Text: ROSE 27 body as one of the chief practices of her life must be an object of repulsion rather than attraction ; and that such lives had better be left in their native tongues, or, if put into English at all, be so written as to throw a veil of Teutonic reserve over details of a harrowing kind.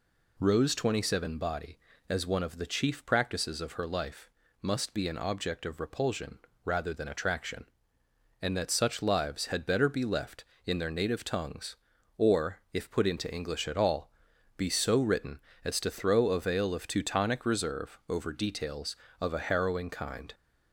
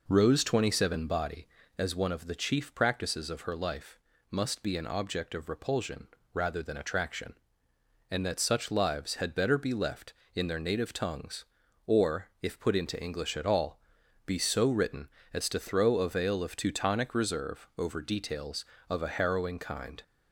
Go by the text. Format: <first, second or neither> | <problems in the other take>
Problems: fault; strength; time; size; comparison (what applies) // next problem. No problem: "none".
first | starts louder than the rest; noticeable; until 1.7 s; 4.5 dB // pauses between "life" and "must"; slight; at 3.9 s; 0.32 s long; slight in the first // pauses between "repulsion" and "rather"; slight; at 6.0 s; 0.26 s long; slight in the first